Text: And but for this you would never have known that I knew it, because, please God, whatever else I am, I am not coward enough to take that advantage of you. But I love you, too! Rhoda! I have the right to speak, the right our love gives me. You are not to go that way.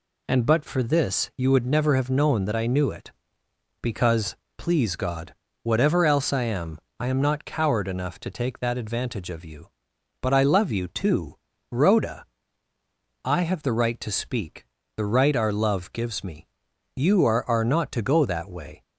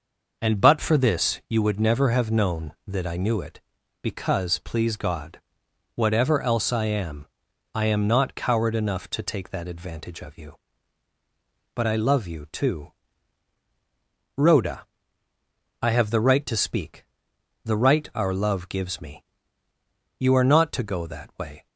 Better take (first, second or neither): second